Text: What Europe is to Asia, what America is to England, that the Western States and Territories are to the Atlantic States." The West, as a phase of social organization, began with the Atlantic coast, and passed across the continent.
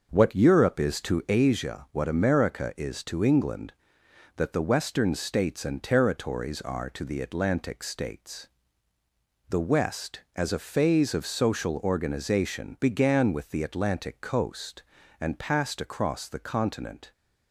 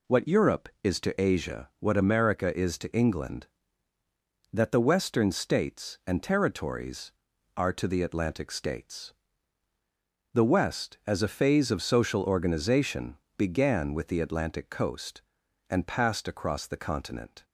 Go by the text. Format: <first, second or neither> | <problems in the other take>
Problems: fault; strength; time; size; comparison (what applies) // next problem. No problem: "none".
second | starts louder than the rest; until 1.3 s; 6 dB